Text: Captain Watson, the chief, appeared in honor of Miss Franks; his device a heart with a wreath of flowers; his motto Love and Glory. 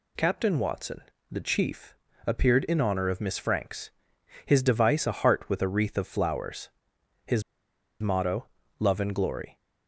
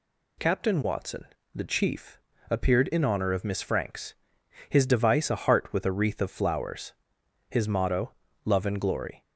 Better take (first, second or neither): second